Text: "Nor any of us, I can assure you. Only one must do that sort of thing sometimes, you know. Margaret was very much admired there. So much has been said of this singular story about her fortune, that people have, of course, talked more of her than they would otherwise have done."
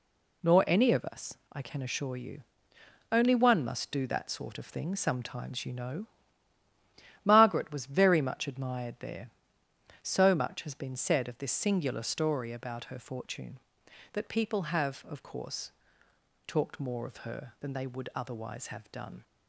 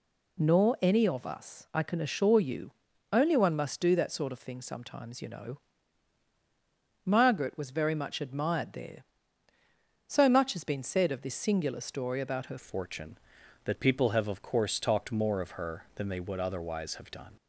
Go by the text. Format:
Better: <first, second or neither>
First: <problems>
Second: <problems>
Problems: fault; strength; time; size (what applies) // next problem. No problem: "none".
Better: first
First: none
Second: changes voice at "fortune"; from 12.5 s on; 4.8 s long